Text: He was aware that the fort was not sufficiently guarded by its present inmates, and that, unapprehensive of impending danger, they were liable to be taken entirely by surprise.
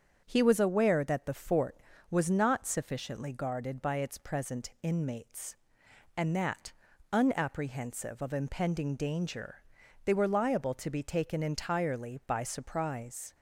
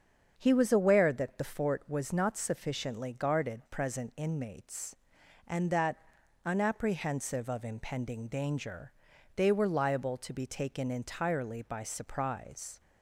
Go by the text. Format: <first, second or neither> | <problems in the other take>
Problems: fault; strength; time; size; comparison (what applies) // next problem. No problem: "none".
first | starts louder than the rest; until 1.3 s; 7 dB; strong in the first // skips "by its"; at 3.6 s